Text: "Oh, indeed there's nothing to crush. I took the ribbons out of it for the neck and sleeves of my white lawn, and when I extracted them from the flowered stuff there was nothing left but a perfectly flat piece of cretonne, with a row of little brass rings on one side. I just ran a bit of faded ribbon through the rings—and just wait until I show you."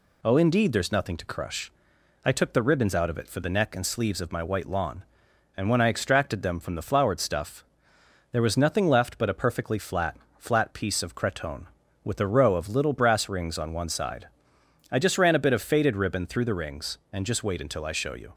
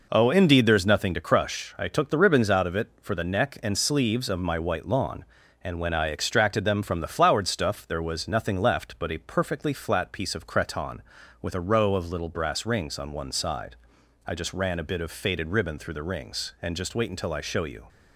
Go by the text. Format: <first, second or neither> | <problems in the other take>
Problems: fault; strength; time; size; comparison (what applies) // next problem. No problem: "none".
second | pauses between "stuff" and "there"; noticeable; at 7.6 s; 0.66 s long // says "flat" twice; at 10.3 s